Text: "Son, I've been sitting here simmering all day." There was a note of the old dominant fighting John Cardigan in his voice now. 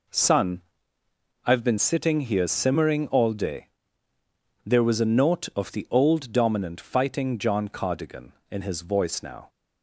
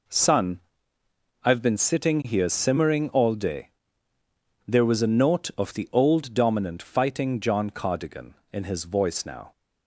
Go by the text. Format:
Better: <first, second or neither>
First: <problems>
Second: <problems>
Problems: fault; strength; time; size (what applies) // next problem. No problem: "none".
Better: neither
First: none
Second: none